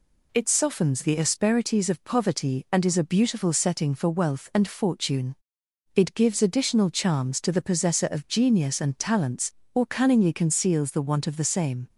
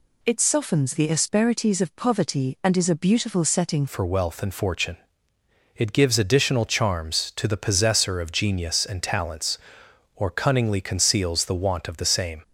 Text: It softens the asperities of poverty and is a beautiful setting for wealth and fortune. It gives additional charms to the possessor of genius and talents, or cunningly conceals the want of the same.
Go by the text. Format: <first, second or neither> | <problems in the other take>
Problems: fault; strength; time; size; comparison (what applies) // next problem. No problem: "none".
first | changes voice at "for"; from 3.8 s on; 8.6 s long